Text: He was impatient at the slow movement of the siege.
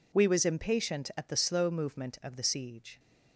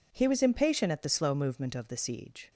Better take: second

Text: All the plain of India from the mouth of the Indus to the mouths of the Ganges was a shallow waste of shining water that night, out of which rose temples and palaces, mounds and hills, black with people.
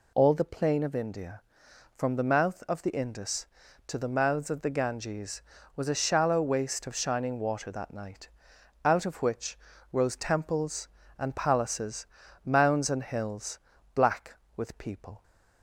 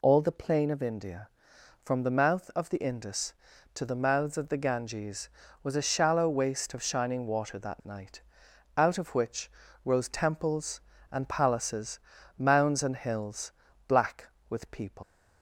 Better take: first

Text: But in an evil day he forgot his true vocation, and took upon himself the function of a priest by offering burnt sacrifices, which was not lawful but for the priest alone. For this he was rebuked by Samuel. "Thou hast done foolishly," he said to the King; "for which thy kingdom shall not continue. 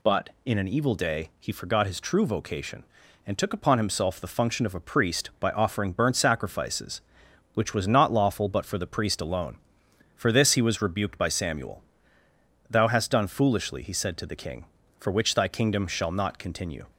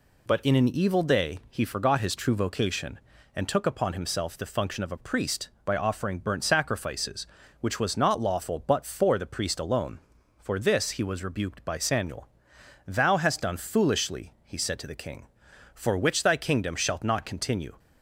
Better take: first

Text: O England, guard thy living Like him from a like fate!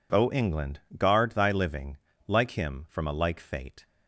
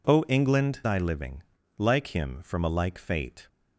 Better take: first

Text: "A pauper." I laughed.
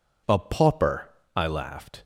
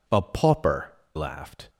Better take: first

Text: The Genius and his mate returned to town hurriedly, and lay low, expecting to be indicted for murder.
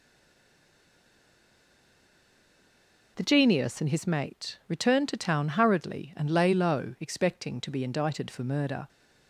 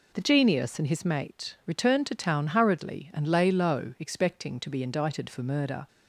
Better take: second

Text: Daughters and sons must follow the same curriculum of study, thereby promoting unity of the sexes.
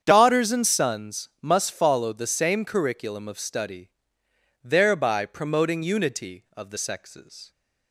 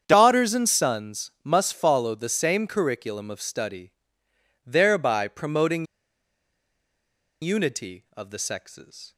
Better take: first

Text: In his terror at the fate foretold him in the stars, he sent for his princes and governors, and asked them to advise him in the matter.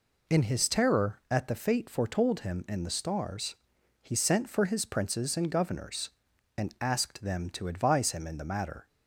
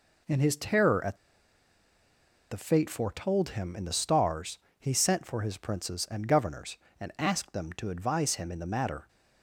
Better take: first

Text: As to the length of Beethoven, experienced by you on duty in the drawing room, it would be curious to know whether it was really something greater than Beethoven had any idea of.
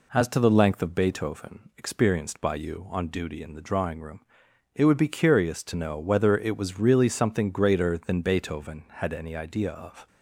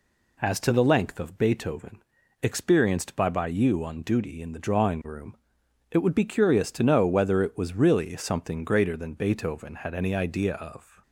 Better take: first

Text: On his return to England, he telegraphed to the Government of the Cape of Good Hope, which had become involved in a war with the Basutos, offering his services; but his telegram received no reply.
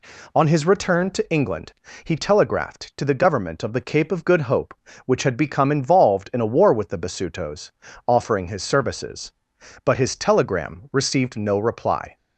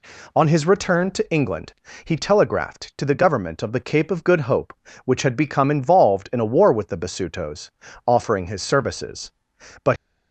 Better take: first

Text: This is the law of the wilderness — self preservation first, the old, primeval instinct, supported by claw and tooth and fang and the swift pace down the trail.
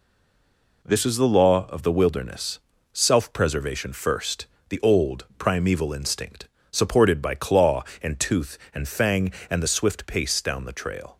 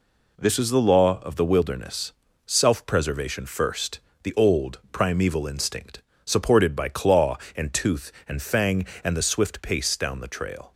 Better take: second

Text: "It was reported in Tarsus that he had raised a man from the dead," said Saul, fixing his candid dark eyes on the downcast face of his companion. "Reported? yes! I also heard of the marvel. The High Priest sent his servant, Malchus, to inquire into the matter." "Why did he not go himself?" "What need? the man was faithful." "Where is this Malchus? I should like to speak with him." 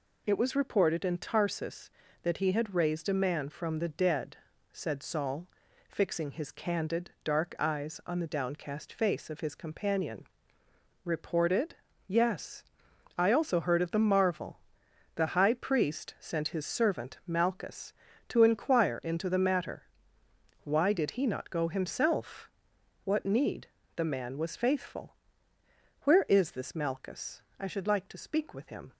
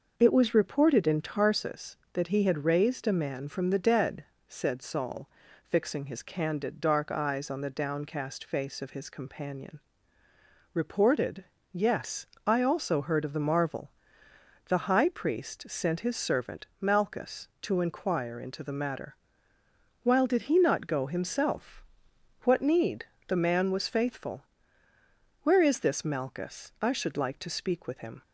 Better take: first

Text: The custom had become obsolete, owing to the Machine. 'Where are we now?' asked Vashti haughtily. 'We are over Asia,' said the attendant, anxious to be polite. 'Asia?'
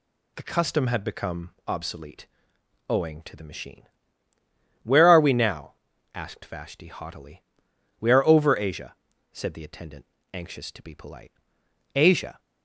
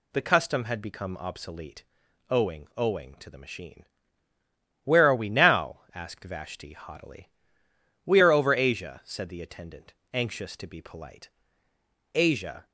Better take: first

